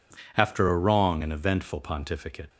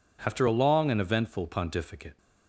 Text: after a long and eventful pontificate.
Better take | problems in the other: second | says "wrong" for "long"; at 0.7 s

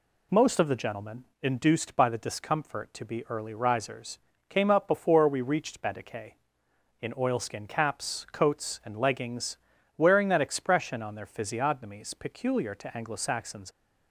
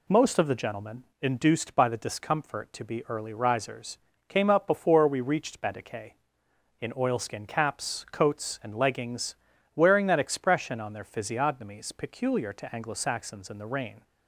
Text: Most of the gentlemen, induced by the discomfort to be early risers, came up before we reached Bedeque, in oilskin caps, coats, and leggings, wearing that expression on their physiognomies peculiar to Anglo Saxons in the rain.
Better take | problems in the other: second | stops before "in the rain"; at 13.7 s

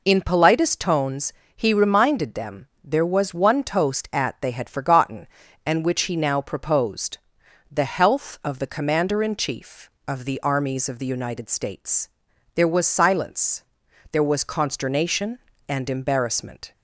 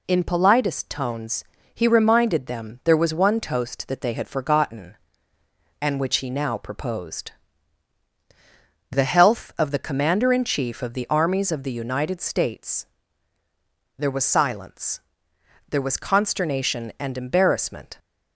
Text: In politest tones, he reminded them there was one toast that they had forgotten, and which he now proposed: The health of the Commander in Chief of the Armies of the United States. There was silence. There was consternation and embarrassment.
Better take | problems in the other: second | pauses between "them" and "there"; slight; at 2.6 s; 0.16 s long // says "at" for "that"; at 4.1 s

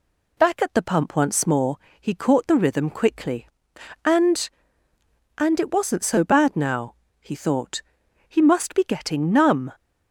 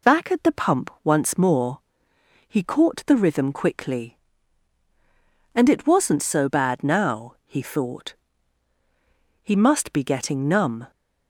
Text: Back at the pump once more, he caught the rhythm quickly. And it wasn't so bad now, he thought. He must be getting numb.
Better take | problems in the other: second | says "And" twice; at 5.3 s

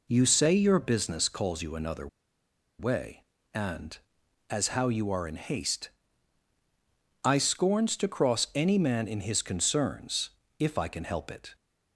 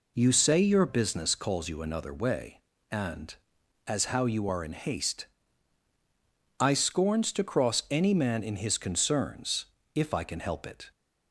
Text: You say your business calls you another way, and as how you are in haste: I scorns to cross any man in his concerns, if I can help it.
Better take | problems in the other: second | pauses between "another" and "way"; noticeable; at 2.0 s; 0.71 s long

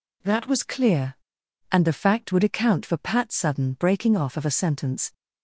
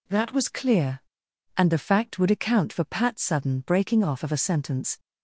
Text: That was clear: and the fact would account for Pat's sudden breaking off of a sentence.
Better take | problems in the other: neither | none

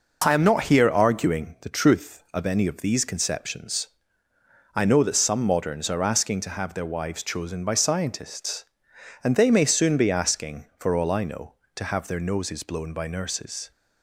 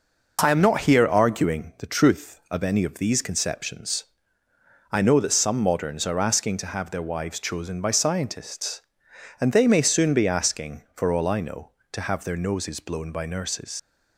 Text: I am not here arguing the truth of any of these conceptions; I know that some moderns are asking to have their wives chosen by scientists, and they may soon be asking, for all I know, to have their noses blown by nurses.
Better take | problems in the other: first | leaves "nurses" unfinished; at 13.7 s; 95 ms

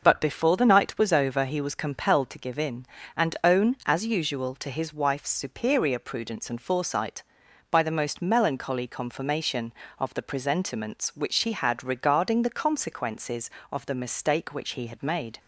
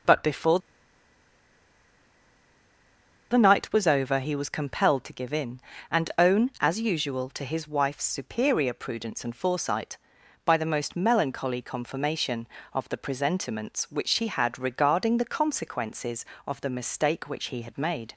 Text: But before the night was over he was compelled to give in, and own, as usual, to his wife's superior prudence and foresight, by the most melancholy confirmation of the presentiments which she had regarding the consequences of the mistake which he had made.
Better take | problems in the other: first | pauses between "before" and "the"; strong; at 0.5 s; 2.7 s long

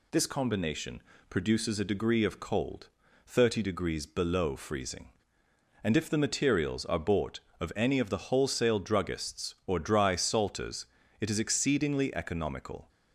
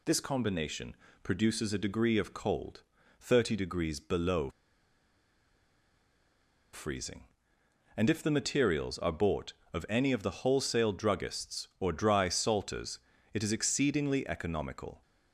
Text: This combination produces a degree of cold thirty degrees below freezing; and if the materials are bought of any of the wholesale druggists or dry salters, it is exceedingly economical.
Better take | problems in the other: first | pauses between "combination" and "produces"; slight; at 0.9 s; 0.28 s long; slight in the first // pauses between "cold" and "thirty"; at 2.8 s; 0.38 s long; also in the first // pauses between "below" and "freezing"; strong; at 4.4 s; 2.2 s long

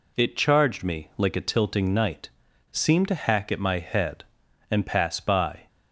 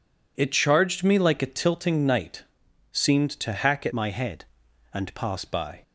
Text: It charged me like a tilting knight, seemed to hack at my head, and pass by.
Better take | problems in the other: first | changes voice from "my" to "pass"; from 3.9 to 5.4 s; 1.5 s long

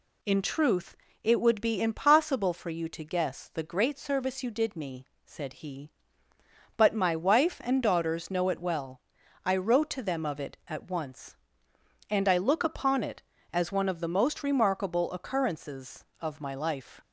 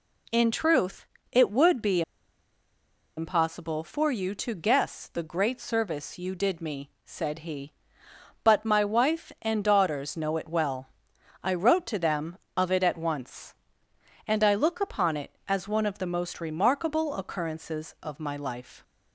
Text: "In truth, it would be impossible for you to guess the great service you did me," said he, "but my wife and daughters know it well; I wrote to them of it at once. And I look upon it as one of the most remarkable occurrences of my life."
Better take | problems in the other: first | pauses between "be" and "impossible"; at 2.0 s; 1.1 s long

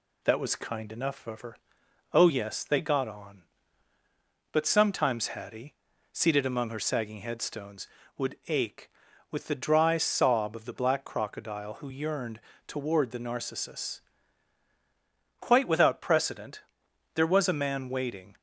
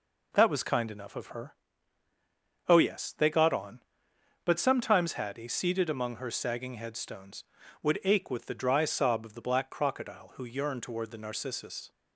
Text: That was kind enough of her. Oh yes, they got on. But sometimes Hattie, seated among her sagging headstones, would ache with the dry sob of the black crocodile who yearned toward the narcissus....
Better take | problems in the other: second | pauses between "yearned" and "toward"; slight; at 12.3 s; 0.26 s long // goes on to say "Quite without precedent there was a man waiting"; strong; from 15.3 s on; 2.9 s long

